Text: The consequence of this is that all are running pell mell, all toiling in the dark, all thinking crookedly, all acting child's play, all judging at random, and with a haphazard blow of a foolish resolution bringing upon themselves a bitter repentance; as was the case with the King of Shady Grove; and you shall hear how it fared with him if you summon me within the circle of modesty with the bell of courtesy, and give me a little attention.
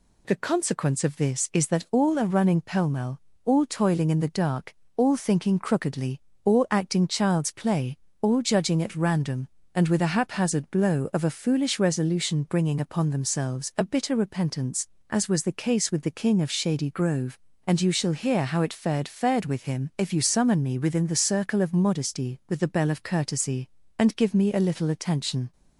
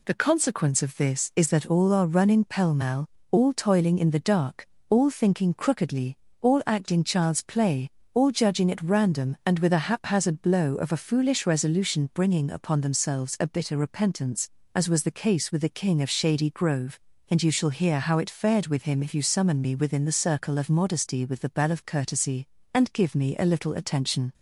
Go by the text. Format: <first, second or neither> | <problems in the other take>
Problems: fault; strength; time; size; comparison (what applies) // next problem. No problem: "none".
second | says "fared" twice; at 19.0 s